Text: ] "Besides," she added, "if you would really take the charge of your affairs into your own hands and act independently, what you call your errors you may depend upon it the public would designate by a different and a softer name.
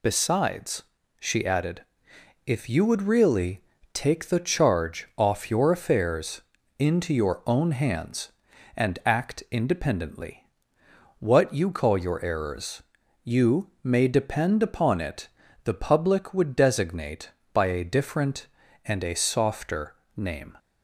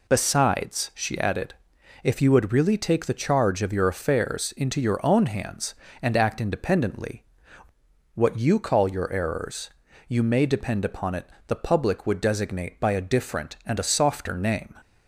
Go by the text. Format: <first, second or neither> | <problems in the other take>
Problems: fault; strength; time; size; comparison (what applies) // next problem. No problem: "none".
second | pauses between "really" and "take"; slight; at 3.6 s; 0.32 s long // says "off" for "of"; at 5.1 s // pauses between "affairs" and "into"; slight; at 6.4 s; 0.36 s long // pauses between "errors" and "you"; at 12.8 s; 0.42 s long; also in the second // pauses between "it" and "the"; slight; at 15.2 s; 0.36 s long; slight in the second // pauses between "softer" and "name"; slight; at 19.9 s; 0.20 s long